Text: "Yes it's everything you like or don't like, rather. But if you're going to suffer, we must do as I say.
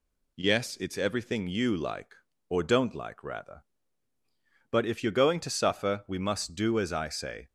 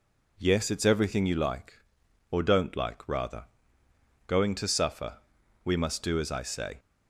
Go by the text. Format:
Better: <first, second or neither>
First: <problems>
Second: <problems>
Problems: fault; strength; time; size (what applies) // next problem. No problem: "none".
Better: first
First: none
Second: skips "But if you're"; at 3.8 s